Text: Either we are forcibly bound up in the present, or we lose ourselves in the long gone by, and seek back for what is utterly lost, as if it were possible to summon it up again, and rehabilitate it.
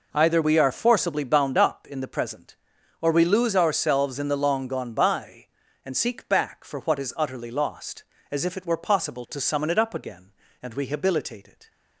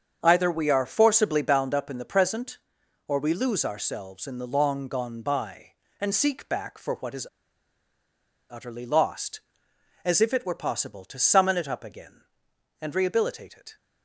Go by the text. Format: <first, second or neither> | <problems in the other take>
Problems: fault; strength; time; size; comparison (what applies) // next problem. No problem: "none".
first | starts louder than the rest; strong; until 1.2 s; 7 dB // pauses between "is" and "utterly"; strong; at 7.2 s; 1.2 s long